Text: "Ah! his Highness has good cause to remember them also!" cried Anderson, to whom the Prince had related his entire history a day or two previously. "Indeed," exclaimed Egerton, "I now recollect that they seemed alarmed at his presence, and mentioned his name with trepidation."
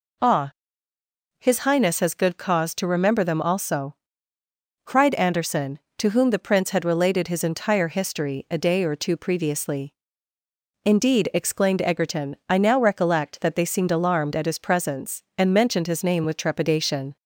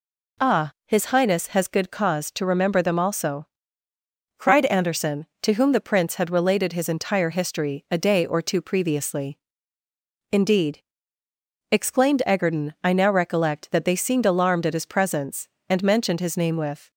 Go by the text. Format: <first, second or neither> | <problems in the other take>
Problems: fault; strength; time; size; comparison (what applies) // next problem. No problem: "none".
first | stops before "trepidation"; at 16.9 s